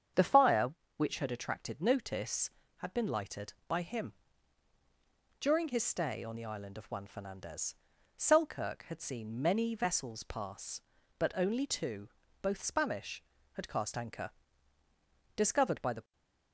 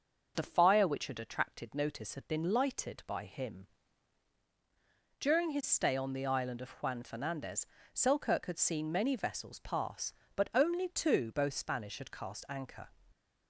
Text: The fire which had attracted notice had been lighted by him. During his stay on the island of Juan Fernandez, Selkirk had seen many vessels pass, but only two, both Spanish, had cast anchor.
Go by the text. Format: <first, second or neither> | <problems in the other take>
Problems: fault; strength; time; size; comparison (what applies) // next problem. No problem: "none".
second | starts louder than the rest; strong; until 1.4 s; 8 dB; noticeable in the second // goes on to say "Discovered by the"; noticeable; from 15.3 s on; 0.76 s long // stays silent after the last word; slight; from 16.0 s on; 0.5 s long